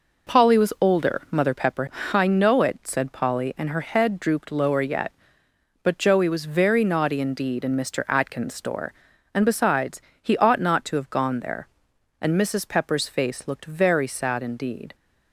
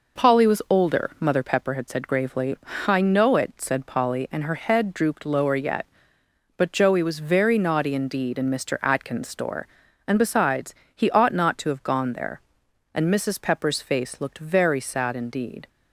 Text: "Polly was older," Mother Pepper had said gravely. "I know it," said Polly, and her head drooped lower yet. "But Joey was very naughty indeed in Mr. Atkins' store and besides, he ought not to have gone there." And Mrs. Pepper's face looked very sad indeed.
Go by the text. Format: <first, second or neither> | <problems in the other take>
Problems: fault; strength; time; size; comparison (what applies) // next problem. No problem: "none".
second | skips "had said gravely"; at 1.9 s